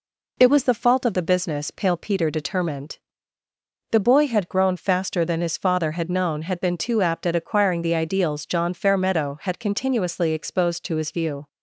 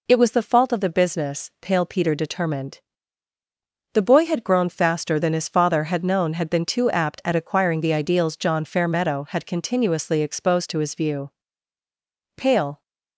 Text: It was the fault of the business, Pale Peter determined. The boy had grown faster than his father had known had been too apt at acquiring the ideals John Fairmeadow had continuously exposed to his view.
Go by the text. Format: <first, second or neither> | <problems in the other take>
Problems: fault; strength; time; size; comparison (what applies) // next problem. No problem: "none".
first | goes on to say "Pale"; slight; from 12.3 s on; 0.46 s long